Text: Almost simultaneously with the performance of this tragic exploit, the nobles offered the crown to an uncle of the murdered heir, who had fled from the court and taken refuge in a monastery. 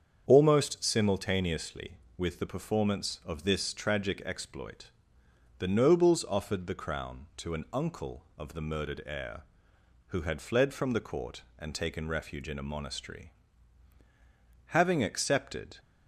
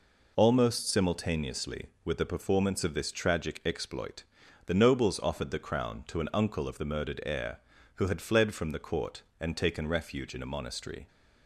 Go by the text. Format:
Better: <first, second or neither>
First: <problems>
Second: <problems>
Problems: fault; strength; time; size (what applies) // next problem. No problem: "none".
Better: second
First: starts louder than the rest; strong; until 1.2 s; 7.5 dB // goes on to say "Having accepted"; noticeable; from 14.6 s on; 1.1 s long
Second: none